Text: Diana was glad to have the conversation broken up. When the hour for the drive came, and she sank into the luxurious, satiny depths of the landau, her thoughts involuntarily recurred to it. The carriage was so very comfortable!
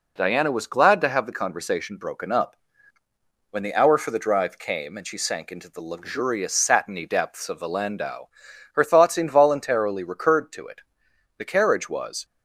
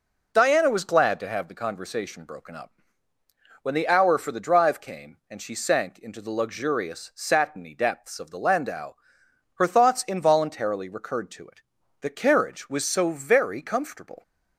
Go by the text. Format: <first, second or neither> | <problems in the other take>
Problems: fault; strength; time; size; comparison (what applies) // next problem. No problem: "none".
second | stops before "so very comfortable"; at 12.2 s